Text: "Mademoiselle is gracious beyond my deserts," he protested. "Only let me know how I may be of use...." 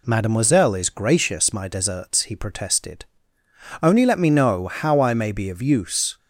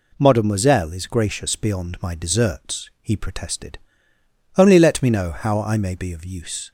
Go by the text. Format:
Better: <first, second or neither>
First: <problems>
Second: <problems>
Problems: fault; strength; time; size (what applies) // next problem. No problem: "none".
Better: second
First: skips "beyond"; at 1.5 s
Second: none